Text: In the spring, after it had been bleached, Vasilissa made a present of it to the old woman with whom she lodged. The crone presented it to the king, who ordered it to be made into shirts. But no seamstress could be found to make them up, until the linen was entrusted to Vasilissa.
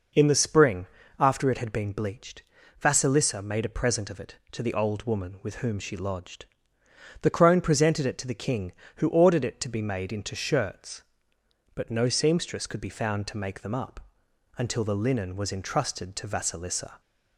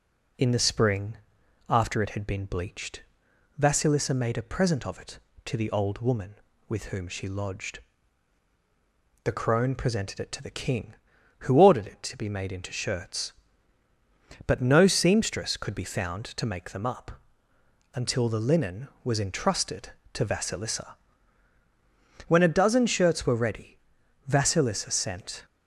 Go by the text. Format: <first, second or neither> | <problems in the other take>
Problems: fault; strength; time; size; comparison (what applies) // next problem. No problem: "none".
first | goes on to say "When a dozen shirts were ready Vasilissa sent"; strong; from 22.2 s on; 3.1 s long